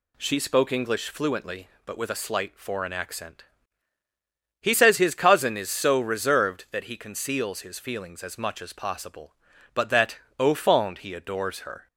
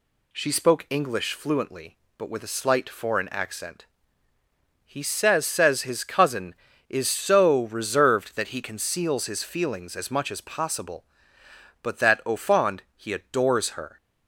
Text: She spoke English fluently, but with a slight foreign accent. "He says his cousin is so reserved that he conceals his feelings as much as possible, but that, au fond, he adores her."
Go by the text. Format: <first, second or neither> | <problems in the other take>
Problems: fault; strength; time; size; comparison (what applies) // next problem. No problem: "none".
first | says "says" twice; at 5.4 s